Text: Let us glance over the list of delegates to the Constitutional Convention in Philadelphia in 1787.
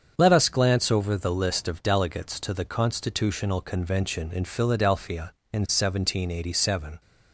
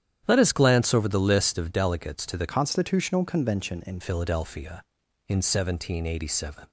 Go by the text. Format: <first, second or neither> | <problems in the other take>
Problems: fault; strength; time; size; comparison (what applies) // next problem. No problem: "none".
first | starts louder than the rest; strong; until 1.2 s; 10 dB; also in the first // changes voice from "Constitutional" to "in"; from 2.4 to 3.9 s; 1.5 s long